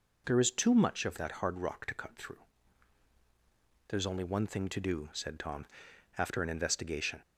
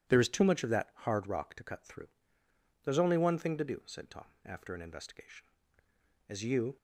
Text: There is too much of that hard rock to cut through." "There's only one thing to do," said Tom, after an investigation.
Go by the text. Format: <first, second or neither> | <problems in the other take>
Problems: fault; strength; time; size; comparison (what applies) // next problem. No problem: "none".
first | goes on to say "As you"; slight; from 6.2 s on; 0.48 s long